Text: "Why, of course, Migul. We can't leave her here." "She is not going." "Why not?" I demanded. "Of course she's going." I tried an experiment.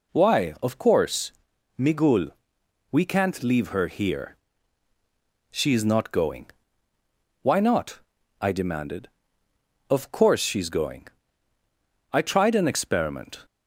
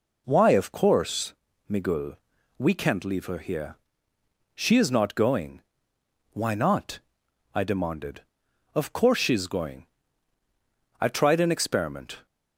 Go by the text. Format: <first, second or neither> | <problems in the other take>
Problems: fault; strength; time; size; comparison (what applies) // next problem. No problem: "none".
neither | none